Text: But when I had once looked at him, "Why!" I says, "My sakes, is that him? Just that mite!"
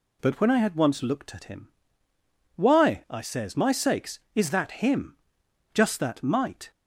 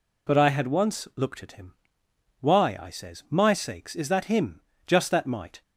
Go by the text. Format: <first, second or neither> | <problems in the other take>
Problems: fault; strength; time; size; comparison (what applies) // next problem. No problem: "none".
first | skips "when"; at 0.3 s